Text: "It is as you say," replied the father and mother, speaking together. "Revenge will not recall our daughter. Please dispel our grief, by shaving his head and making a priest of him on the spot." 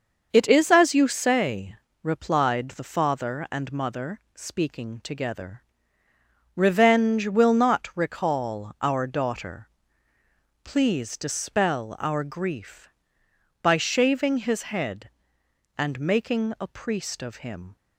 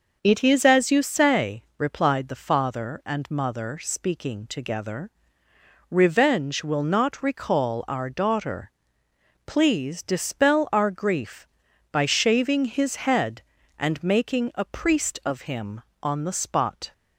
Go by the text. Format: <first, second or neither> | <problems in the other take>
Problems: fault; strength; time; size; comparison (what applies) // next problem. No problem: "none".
second | starts louder than the rest; until 1.3 s; 6.5 dB // stops before "on the spot"; at 17.7 s